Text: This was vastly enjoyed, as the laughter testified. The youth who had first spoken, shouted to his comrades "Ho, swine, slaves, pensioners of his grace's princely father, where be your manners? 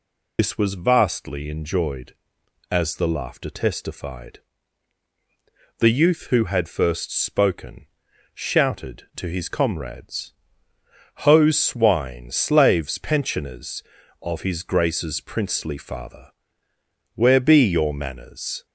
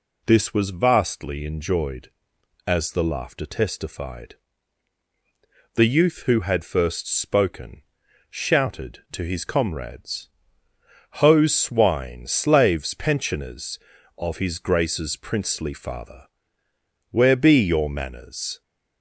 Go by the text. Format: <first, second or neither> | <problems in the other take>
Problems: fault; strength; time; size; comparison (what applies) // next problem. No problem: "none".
second | loses the start of "This"; at 0.3 s; 100 ms // pauses between "comrades" and "Ho"; noticeable; at 10.3 s; 0.90 s long; noticeable in the second